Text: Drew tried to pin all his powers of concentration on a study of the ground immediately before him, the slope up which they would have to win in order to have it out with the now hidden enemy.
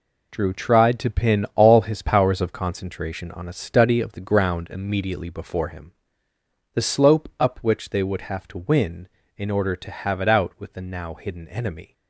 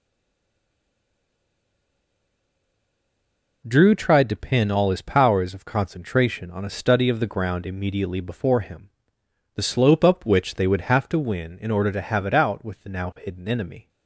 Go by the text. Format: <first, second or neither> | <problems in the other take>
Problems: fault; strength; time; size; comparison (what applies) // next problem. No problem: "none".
first | stays silent before the first word; strong; until 3.6 s; 3.6 s long